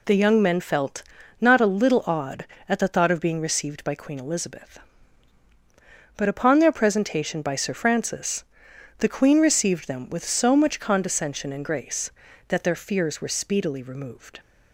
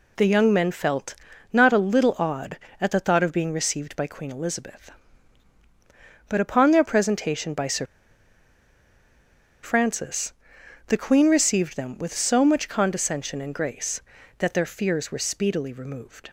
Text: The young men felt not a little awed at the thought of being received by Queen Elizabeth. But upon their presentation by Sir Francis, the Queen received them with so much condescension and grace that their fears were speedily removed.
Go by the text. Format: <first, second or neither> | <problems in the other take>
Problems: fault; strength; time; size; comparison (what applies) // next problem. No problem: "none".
first | pauses between "felt" and "not"; at 1.1 s; 0.38 s long; also in the first // pauses between "Sir" and "Francis"; strong; at 7.8 s; 1.7 s long